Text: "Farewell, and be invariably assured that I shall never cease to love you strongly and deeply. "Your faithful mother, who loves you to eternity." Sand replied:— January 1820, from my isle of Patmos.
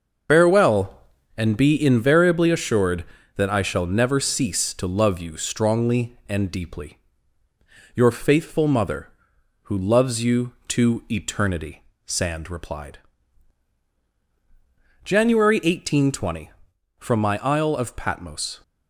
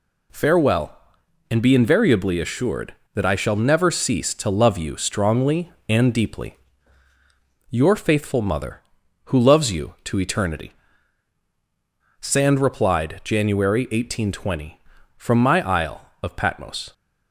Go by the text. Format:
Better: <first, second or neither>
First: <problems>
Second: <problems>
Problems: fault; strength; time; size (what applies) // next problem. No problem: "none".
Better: second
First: loses the start of "Farewell"; at 0.2 s; 85 ms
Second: none